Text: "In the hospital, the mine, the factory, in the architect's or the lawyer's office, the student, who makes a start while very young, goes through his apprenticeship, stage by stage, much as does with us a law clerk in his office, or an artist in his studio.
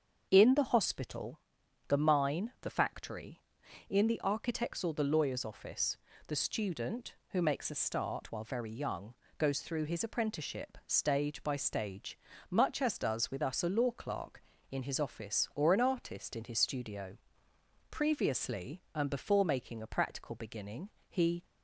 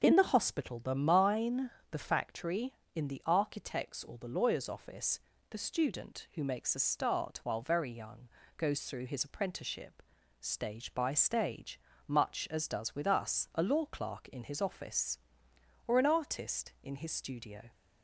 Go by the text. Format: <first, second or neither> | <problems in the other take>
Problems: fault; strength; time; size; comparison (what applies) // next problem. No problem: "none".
second | starts louder than the rest; until 1.3 s; 7 dB; also in the second // goes on to say "Previously and before making a practical beginning he"; strong; from 17.8 s on; 3.5 s long